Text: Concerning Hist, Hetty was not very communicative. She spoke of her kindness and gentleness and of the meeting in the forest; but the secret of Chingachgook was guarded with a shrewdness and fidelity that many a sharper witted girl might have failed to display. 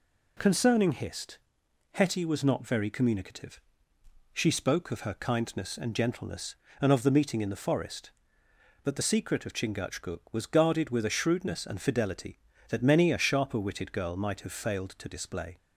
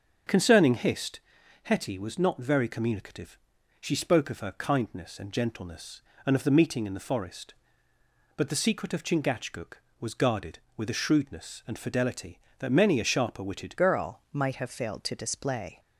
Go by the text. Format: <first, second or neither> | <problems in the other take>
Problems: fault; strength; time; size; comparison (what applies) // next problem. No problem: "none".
first | starts louder than the rest; noticeable; until 1.7 s; 6 dB // changes voice at "girl"; from 13.7 s on; 2.0 s long